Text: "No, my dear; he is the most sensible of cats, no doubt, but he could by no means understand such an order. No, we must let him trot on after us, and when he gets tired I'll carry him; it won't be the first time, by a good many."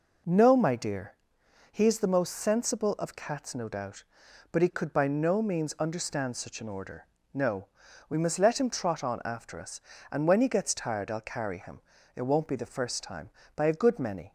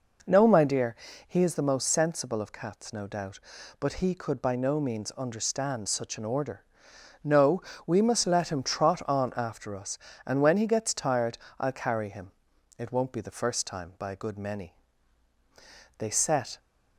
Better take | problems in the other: first | pauses between "tired" and "I'll"; slight; at 11.3 s; 0.20 s long // goes on to say "They set"; noticeable; from 15.9 s on; 0.62 s long

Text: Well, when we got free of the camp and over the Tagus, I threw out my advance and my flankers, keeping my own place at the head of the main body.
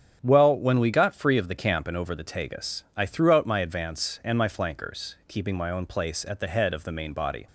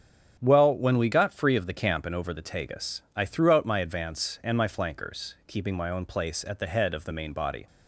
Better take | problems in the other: neither | starts louder than the rest; strong; the same in both

